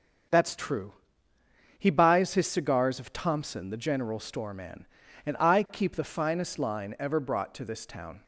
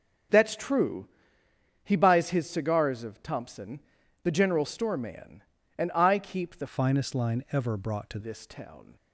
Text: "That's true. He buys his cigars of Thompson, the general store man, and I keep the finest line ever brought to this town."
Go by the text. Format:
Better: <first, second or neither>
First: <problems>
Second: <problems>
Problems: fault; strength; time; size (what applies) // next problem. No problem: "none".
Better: first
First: starts louder than the rest; until 2.1 s; 6.5 dB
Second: starts louder than the rest; until 2.0 s; 6.5 dB // changes voice from "finest" to "to"; from 6.6 to 8.1 s; 1.5 s long